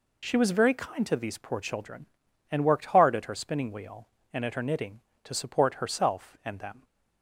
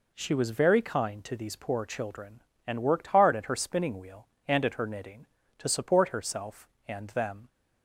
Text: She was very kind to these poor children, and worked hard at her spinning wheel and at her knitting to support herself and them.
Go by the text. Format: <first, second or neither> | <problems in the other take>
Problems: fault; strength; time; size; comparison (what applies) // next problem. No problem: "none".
neither | none